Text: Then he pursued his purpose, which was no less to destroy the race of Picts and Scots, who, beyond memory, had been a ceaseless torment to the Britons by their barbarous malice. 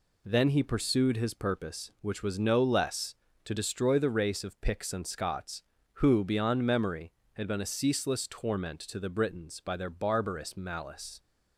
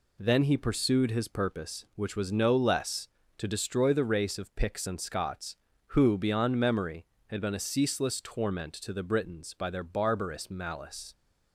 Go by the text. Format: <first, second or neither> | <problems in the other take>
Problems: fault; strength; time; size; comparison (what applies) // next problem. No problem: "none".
neither | none